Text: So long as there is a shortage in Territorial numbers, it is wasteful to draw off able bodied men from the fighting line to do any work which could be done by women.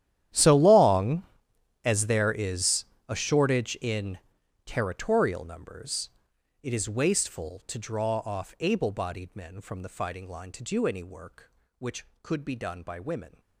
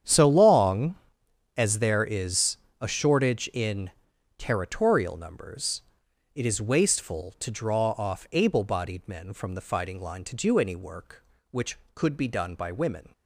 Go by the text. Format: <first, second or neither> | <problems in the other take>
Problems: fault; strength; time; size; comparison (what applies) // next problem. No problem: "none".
second | gets quieter; strong; throughout; 20.5 dB // starts louder than the rest; strong; until 1.9 s; 11.5 dB; strong in the second // pauses between "is" and "a"; slight; at 2.8 s; 0.22 s long; slight in the second // pauses between "in" and "Territorial"; noticeable; at 4.1 s; 0.48 s long; noticeable in the second